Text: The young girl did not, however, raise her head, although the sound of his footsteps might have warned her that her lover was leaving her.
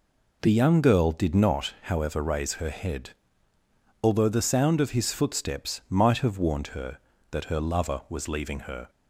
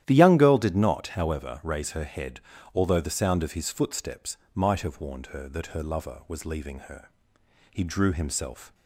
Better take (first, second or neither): first